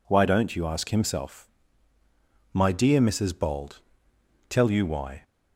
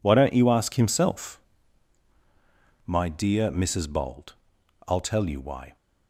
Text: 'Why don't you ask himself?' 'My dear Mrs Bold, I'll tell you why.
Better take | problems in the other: second | skips "I'll"; at 4.1 s

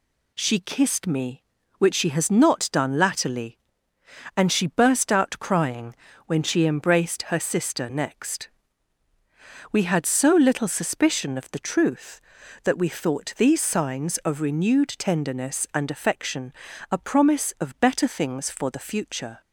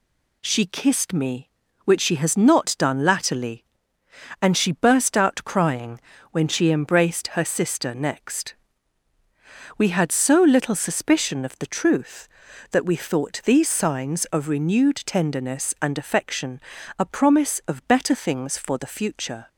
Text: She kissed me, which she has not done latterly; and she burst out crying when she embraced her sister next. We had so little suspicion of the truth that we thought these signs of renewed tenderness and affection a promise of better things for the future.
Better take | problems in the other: neither | pauses between "crying" and "when"; slight; the same in both // pauses between "affection" and "a"; the same in both

